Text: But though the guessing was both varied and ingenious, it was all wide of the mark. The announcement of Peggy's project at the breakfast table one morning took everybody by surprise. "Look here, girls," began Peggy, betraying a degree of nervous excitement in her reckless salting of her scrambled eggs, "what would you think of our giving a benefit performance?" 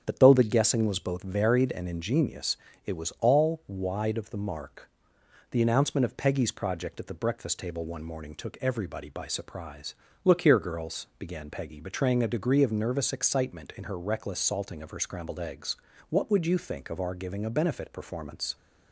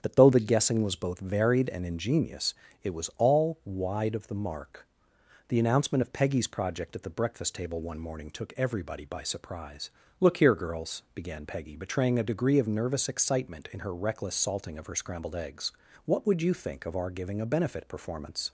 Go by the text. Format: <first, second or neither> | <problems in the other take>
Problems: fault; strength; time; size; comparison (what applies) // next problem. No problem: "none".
neither | starts louder than the rest; strong; the same in both